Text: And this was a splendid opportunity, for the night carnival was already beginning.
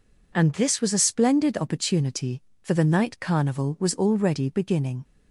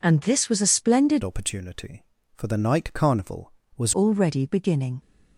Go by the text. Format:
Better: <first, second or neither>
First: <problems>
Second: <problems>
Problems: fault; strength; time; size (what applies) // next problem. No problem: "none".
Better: first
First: none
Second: changes voice from "opportunity" to "was"; from 1.2 to 3.9 s; 2.7 s long